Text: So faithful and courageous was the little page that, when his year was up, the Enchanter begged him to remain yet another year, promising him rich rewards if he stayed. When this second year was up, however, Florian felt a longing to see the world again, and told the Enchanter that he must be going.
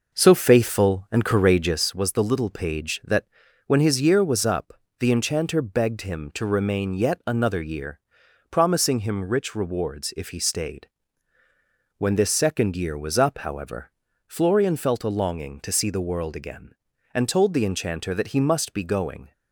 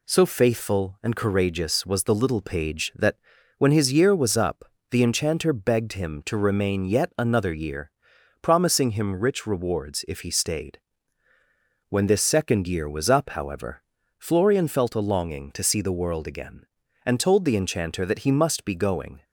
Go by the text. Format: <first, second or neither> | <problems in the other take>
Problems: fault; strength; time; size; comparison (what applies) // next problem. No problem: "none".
second | starts louder than the rest; noticeable; until 1.9 s; 5.5 dB